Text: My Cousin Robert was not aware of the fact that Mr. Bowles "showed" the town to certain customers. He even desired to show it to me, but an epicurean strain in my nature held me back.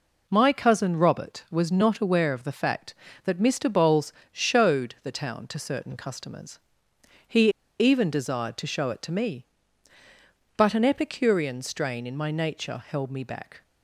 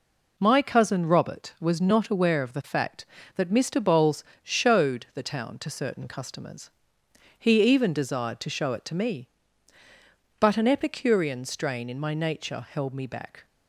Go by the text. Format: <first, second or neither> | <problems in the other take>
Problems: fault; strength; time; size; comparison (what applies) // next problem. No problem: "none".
second | pauses between "Bowles" and "showed"; slight; at 4.1 s; 0.22 s long; slight in the second // pauses between "He" and "even"; slight; at 7.4 s; 0.30 s long